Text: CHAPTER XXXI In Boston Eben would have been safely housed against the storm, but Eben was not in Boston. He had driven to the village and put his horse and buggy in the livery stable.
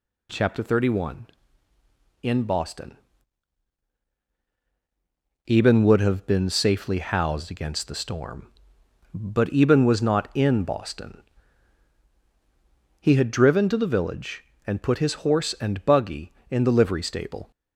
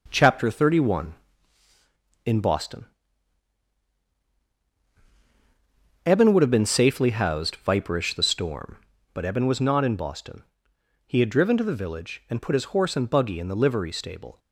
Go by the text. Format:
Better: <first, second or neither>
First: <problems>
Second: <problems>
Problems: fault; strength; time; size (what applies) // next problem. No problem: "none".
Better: first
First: pauses between "Boston" and "Eben"; strong; at 2.9 s; 2.5 s long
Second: pauses between "Boston" and "Eben"; strong; at 2.8 s; 3.2 s long // says "viperish" for "against"; at 7.6 s